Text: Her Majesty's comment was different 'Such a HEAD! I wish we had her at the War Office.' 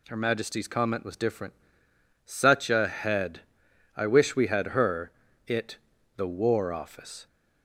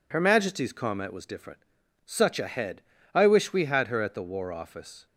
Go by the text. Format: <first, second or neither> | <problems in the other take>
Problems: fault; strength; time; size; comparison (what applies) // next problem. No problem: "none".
second | pauses between "different" and "Such"; noticeable; at 1.5 s; 0.72 s long; also in the second // says "it" for "at"; at 5.4 s